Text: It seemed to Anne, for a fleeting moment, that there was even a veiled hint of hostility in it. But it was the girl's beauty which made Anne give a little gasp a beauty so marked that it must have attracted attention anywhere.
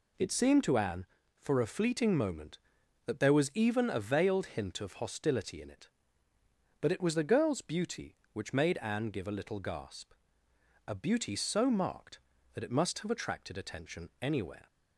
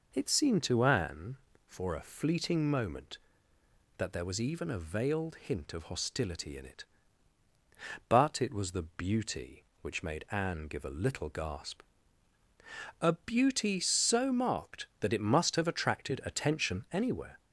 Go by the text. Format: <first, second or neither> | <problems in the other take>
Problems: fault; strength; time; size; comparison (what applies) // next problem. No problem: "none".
first | skips "girl's"; at 8.8 s // pauses between "gasp" and "a"; at 11.8 s; 1.1 s long; noticeable in the first